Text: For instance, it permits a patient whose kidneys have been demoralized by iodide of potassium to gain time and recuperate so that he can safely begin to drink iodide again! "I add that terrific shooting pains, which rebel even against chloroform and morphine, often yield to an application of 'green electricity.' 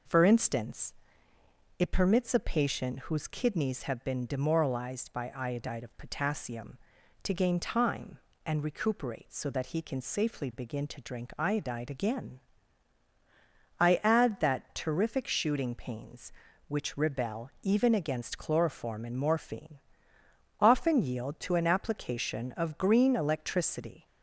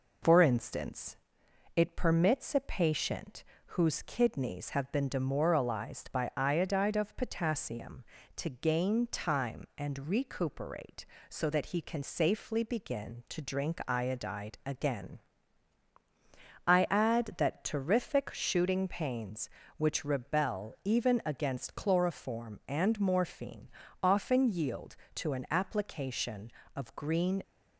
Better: first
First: none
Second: pauses between "patient" and "whose"; slight; at 3.4 s; 0.24 s long // stops before "electricity"; at 27.4 s

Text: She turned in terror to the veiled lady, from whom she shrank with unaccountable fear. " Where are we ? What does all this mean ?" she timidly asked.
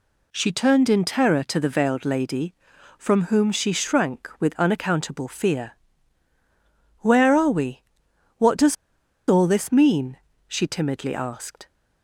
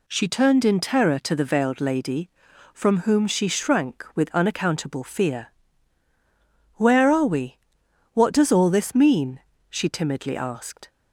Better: second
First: pauses between "does" and "all"; noticeable; at 8.7 s; 0.54 s long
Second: none

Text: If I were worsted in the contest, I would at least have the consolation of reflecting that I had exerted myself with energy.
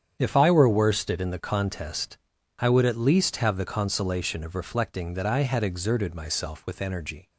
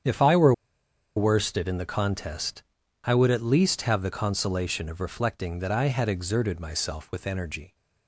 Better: first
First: starts louder than the rest; strong; until 1.2 s; 8.5 dB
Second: starts louder than the rest; strong; until 1.6 s; 8.5 dB // pauses between "were" and "worsted"; noticeable; at 0.5 s; 0.63 s long

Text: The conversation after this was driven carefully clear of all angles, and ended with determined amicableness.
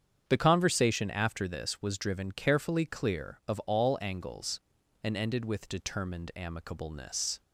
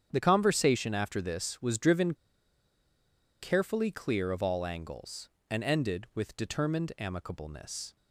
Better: first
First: starts louder than the rest; strong; until 1.2 s; 8 dB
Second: starts louder than the rest; strong; until 1.1 s; 8.5 dB // pauses between "driven" and "carefully"; strong; at 2.1 s; 1.2 s long

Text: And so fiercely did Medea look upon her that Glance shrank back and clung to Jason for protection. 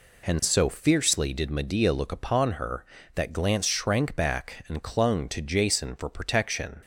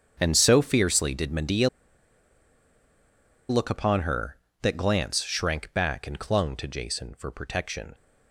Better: first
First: none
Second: starts louder than the rest; strong; until 1.2 s; 7.5 dB // pauses between "Medea" and "look"; strong; at 1.6 s; 1.8 s long

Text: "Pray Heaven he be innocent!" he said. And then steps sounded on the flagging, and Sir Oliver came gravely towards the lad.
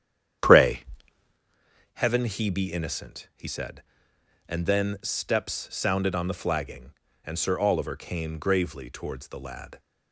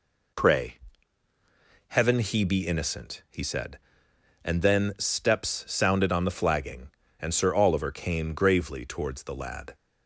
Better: second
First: starts louder than the rest; strong; until 1.4 s; 9.5 dB // pauses between "Pray" and "Heaven"; at 0.8 s; 1.1 s long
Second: pauses between "Pray" and "Heaven"; at 0.7 s; 1.1 s long

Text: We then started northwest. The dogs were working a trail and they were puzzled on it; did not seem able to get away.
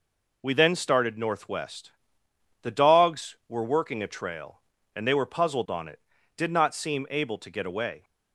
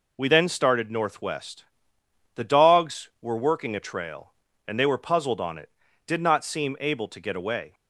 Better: neither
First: none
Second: none

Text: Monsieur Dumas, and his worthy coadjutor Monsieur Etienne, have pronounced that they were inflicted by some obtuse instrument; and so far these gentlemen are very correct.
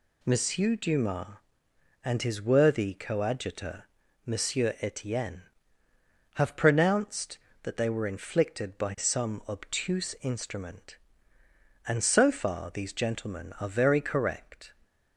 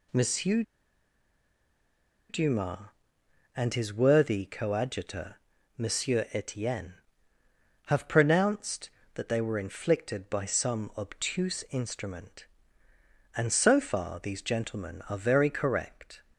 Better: first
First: pauses between "coadjutor" and "Monsieur"; at 3.8 s; 0.38 s long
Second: pauses between "Monsieur" and "Dumas"; strong; at 0.6 s; 1.6 s long // pauses between "coadjutor" and "Monsieur"; at 5.3 s; 0.38 s long

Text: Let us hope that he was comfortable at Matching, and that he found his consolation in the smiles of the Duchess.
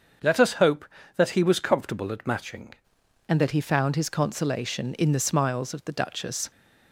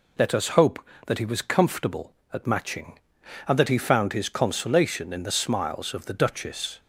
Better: second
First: starts louder than the rest; until 1.5 s; 7 dB // changes voice at "and"; from 3.2 s on; 3.3 s long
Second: none

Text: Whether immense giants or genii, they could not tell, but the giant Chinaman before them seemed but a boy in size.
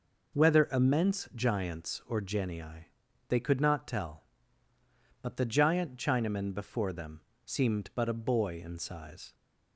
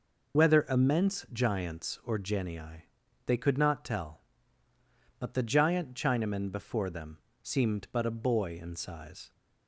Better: first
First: pauses between "them" and "seemed"; slight; at 7.1 s; 0.26 s long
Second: loses the start of "Whether"; at 0.3 s; 35 ms // pauses between "them" and "seemed"; slight; at 7.1 s; 0.26 s long

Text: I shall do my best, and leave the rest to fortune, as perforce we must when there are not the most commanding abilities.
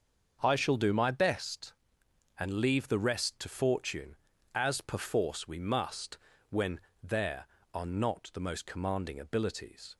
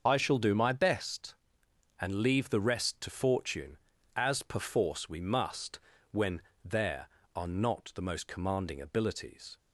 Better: first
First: starts louder than the rest; until 1.4 s; 6.5 dB // pauses between "must" and "when"; slight; at 6.1 s; 0.32 s long // pauses between "when" and "there"; slight; at 6.7 s; 0.24 s long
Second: loses the start of "I"; at 0.0 s; 50 ms // starts louder than the rest; until 1.0 s; 6.5 dB // pauses between "must" and "when"; slight; at 5.7 s; 0.32 s long // pauses between "when" and "there"; slight; at 6.4 s; 0.24 s long

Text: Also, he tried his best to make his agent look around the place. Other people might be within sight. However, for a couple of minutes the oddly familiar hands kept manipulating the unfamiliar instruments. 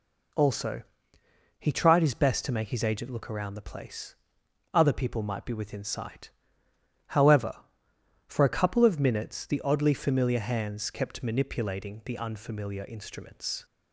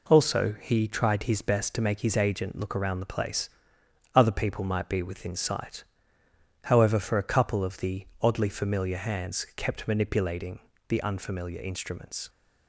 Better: first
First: none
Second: skips "minutes"; at 7.7 s // pauses between "manipulating" and "the"; slight; at 10.5 s; 0.30 s long

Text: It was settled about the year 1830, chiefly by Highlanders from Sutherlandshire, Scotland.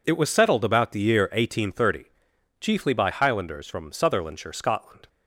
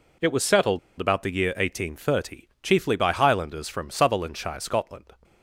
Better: first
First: none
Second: pauses between "settled" and "about"; slight; at 0.7 s; 0.21 s long

